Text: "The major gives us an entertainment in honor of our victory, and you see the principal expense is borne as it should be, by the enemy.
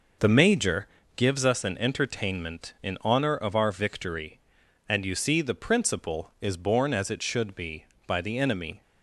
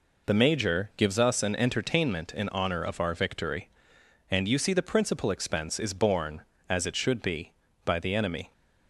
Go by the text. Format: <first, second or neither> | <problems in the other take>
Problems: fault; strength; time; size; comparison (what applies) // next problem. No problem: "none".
second | pauses between "major" and "gives"; slight; at 0.8 s; 0.30 s long // skips "expense"; at 6.3 s